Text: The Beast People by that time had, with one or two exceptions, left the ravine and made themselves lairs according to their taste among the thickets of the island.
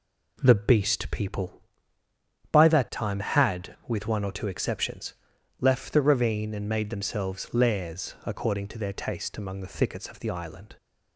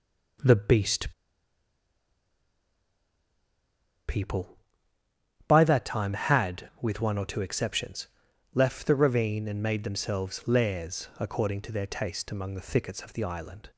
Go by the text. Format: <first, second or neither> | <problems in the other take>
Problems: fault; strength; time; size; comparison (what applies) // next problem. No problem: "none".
first | pauses between "Beast" and "People"; strong; at 1.1 s; 2.9 s long